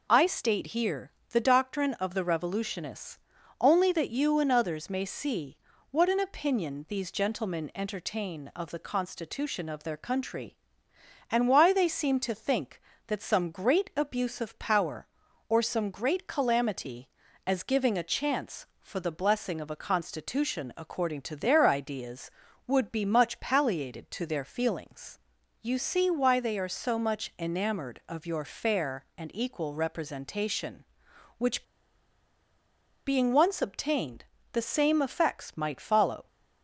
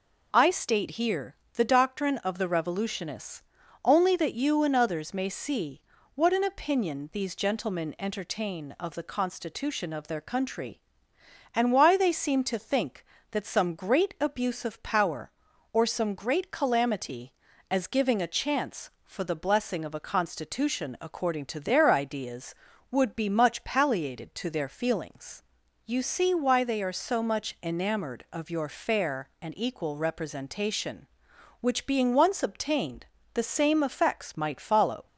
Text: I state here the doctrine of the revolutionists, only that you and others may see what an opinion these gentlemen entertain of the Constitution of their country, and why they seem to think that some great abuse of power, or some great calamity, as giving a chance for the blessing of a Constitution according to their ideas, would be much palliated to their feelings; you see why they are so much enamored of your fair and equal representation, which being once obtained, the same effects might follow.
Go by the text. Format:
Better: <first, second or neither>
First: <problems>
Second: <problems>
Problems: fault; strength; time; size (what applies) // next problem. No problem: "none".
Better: second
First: pauses between "here" and "the"; slight; at 1.1 s; 0.20 s long // pauses between "see" and "what"; slight; at 5.5 s; 0.34 s long // pauses between "which" and "being"; strong; at 31.6 s; 1.4 s long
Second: pauses between "here" and "the"; slight; at 1.3 s; 0.20 s long // pauses between "see" and "what"; slight; at 5.8 s; 0.34 s long